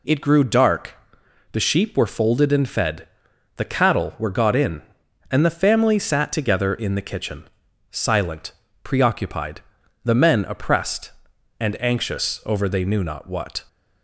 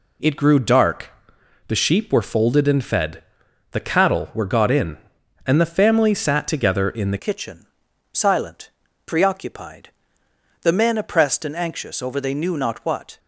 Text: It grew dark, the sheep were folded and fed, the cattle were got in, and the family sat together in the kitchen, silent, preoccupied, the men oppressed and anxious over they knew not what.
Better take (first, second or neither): first